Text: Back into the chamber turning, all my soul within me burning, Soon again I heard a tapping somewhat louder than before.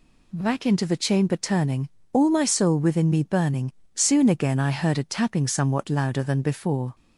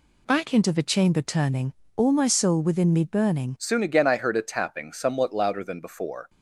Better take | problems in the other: first | changes voice at "Soon"; from 3.5 s on; 2.7 s long

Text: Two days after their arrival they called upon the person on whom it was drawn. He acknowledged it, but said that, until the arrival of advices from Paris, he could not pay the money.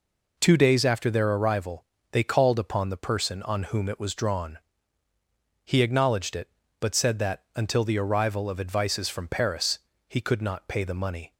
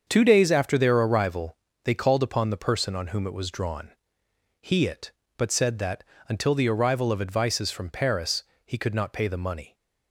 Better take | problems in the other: first | starts louder than the rest; until 1.0 s; 7 dB // pauses between "arrival" and "they"; slight; at 1.5 s; 0.28 s long; slight in the first // skips "acknowledged"; at 4.8 s

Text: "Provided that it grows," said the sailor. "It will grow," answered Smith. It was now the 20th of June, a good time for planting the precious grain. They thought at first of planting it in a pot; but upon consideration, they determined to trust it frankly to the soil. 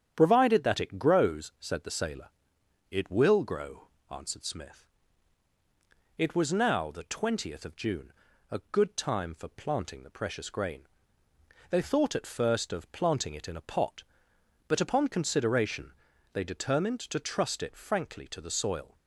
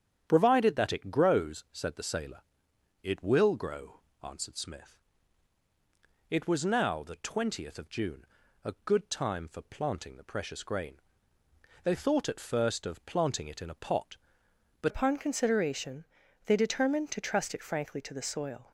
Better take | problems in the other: first | starts louder than the rest; strong; until 1.3 s; 9 dB; strong in the first // changes voice at "upon"; from 14.8 s on; 3.9 s long

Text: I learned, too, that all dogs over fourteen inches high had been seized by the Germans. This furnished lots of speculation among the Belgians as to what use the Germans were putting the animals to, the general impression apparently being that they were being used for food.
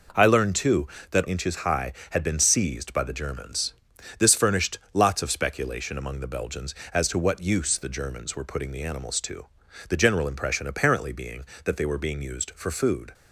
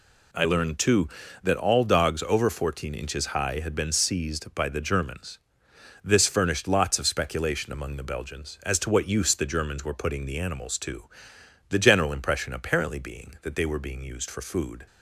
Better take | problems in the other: second | skips "all dogs over fourteen"; at 1.2 s // pauses between "furnished" and "lots"; slight; at 4.7 s; 0.16 s long

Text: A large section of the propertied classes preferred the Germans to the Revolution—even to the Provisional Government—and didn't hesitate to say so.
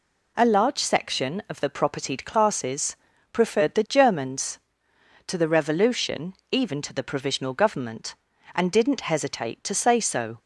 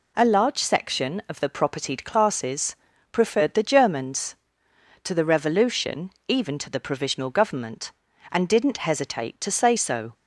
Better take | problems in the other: neither | pauses between "classes" and "preferred"; slight; the same in both

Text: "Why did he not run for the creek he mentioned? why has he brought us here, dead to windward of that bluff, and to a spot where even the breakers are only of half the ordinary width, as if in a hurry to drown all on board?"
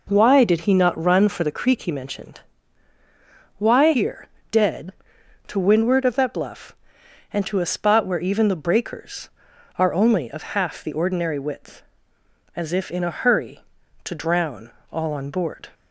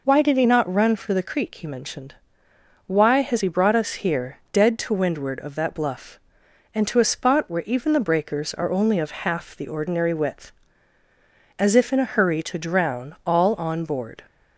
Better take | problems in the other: second | skips "has he brought us"; at 3.9 s // pauses between "of" and "half"; slight; at 10.4 s; 0.16 s long // pauses between "drown" and "all"; slight; at 14.7 s; 0.20 s long

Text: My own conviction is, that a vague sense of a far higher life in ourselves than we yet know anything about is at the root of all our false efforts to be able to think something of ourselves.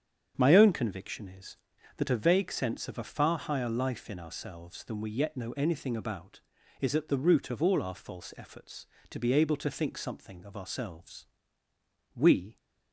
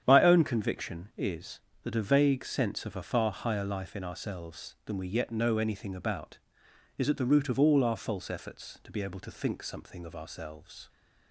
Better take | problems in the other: second | starts louder than the rest; strong; until 1.3 s; 7.5 dB; strong in the second // goes on to say "We"; slight; from 12.1 s on; 0.40 s long

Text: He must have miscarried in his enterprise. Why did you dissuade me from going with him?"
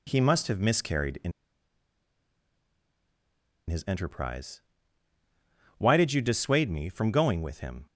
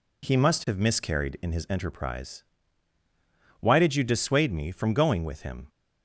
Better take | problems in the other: second | pauses between "in" and "his"; strong; at 1.3 s; 2.3 s long

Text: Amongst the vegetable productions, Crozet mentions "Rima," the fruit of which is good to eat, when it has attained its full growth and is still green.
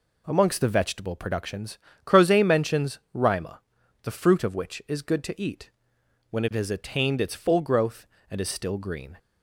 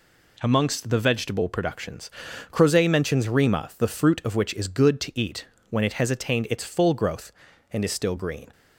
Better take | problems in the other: neither | none

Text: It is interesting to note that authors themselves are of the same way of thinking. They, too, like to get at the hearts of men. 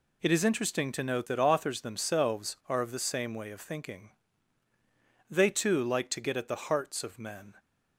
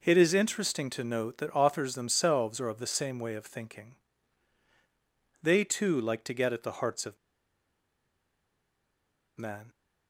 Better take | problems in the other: first | pauses between "of" and "men"; strong; at 7.1 s; 2.2 s long

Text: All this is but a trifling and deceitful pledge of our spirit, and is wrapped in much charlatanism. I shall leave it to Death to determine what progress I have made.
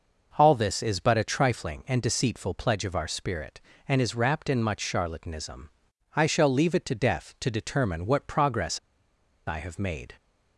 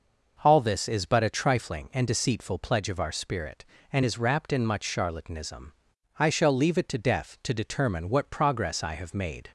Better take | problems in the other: second | pauses between "progress" and "I"; noticeable; at 8.7 s; 0.68 s long

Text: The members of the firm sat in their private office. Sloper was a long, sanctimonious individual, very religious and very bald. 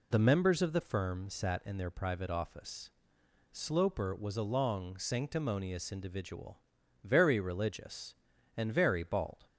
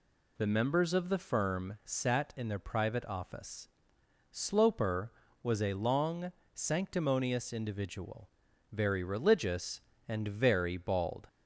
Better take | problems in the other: neither | none

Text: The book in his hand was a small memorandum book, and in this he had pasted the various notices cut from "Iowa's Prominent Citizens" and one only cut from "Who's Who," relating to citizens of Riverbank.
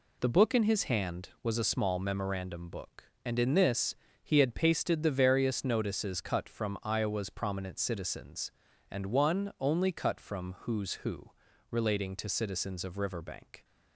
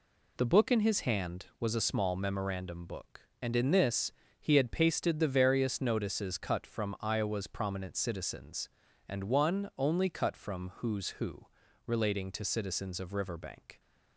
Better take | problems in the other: neither | pauses between "this" and "he"; slight; the same in both

